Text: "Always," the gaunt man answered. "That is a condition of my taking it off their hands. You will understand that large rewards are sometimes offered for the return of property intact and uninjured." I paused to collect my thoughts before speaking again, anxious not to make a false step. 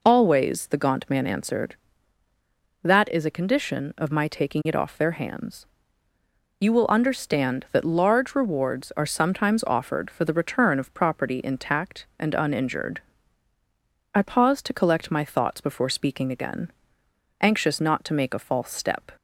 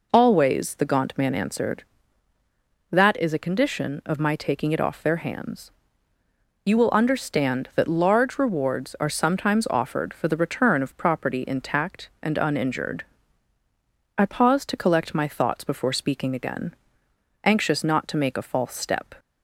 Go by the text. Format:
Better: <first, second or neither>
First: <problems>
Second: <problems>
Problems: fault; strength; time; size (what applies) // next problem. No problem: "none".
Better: neither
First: none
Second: none